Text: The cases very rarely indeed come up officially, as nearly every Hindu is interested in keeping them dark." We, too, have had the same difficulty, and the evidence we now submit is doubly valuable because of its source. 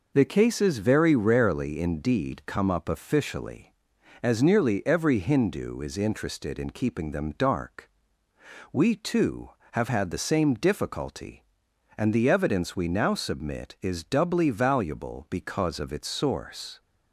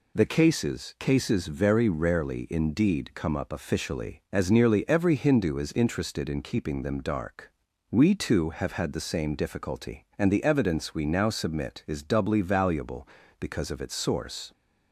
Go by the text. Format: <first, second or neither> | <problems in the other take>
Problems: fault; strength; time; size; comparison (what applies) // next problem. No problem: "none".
first | says "cases" twice; at 0.9 s